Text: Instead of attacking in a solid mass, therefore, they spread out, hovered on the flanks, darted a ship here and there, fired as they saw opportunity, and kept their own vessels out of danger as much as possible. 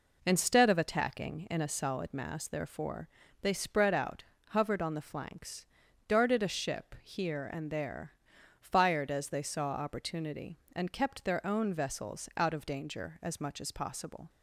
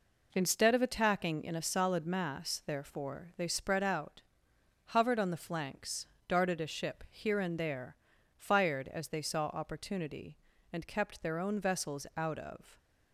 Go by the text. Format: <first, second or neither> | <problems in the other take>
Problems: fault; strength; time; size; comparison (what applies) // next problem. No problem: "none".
first | stops before "danger as much as possible"; at 12.7 s